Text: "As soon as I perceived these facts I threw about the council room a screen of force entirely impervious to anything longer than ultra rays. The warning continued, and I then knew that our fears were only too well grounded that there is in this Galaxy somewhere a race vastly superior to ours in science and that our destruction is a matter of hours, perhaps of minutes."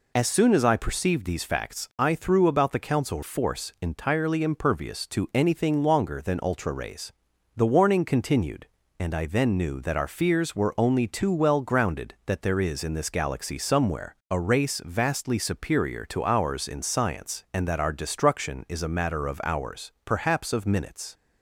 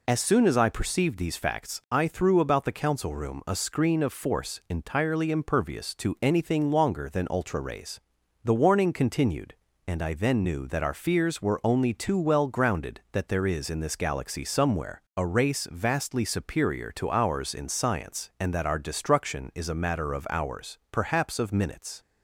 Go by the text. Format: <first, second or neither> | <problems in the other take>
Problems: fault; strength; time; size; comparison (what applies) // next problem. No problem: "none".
second | skips "room a screen of"; at 3.2 s // pauses between "somewhere" and "a"; slight; at 14.1 s; 0.16 s long; slight in the second